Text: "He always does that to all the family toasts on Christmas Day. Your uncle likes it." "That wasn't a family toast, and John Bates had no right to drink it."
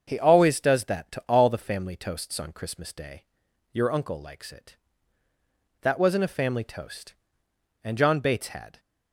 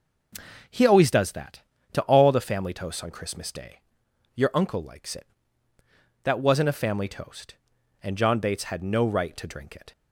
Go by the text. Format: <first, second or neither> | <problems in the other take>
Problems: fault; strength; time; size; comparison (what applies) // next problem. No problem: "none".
second | starts louder than the rest; until 1.0 s; 7 dB // stops before "no right to drink it"; at 8.7 s